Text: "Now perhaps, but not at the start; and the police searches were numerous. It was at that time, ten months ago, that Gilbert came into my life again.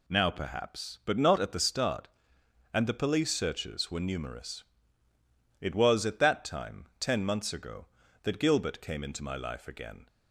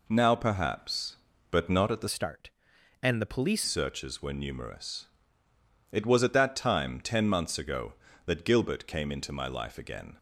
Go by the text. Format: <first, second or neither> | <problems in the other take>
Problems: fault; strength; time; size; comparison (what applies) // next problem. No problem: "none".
first | changes voice from "start" to "police"; from 2.0 to 3.6 s; 1.6 s long